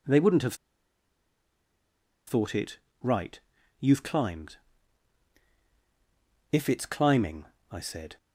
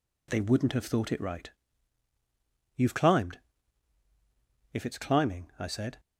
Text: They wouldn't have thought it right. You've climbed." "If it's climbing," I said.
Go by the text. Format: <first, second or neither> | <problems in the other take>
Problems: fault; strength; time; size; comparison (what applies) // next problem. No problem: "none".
second | pauses between "have" and "thought"; strong; at 0.5 s; 1.7 s long // pauses between "it" and "right"; slight; at 2.7 s; 0.24 s long